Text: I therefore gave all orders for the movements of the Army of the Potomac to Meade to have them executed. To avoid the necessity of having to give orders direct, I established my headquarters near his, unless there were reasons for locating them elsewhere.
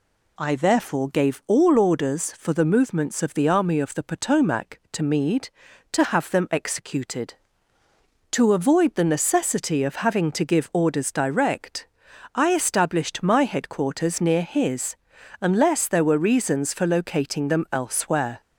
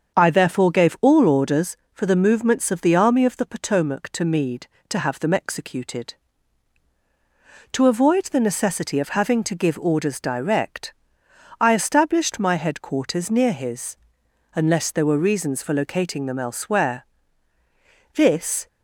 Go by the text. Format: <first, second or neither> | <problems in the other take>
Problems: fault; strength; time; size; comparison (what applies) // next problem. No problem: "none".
first | starts louder than the rest; until 1.1 s; 7 dB // goes on to say "This"; from 18.1 s on; 0.54 s long